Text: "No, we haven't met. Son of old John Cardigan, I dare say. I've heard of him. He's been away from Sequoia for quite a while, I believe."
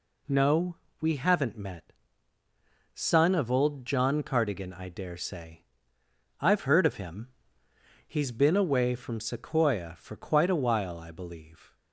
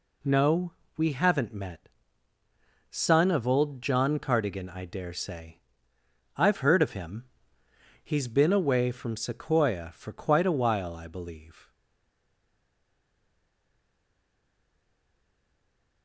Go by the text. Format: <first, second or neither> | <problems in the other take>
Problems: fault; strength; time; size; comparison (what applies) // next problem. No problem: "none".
first | stays silent after the last word; strong; from 11.7 s on; 4.3 s long